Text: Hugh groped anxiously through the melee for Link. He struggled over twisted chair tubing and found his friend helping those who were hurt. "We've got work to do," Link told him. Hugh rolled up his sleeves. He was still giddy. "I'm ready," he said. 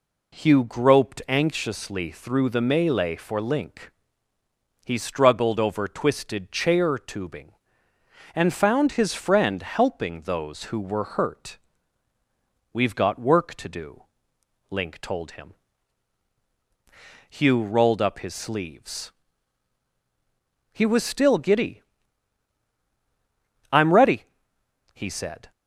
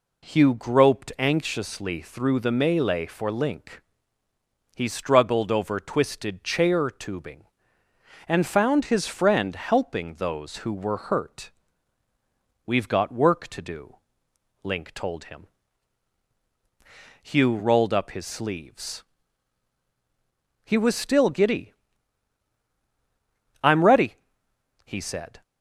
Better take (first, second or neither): neither